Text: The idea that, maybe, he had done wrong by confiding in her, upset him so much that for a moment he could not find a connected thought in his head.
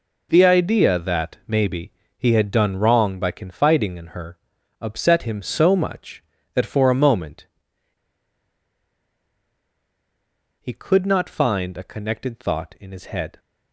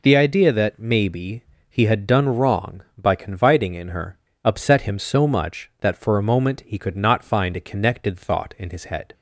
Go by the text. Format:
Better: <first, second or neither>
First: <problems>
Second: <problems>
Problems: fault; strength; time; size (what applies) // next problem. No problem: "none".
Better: second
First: pauses between "moment" and "he"; strong; at 7.4 s; 3.1 s long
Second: none